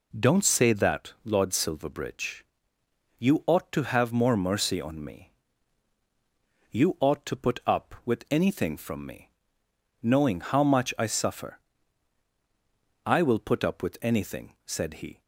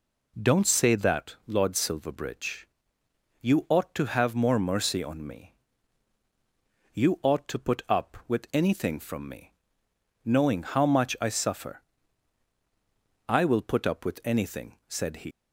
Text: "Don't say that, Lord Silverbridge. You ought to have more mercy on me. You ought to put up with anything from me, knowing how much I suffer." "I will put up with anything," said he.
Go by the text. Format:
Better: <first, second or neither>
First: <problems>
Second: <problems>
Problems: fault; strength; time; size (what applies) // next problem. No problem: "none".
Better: first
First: none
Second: leaves "he" unfinished; at 15.3 s; 125 ms